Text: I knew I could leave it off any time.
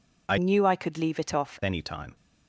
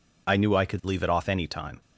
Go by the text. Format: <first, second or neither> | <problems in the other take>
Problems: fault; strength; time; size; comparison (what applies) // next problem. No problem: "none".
second | changes voice from "knew" to "off"; from 0.3 to 1.5 s; 1.2 s long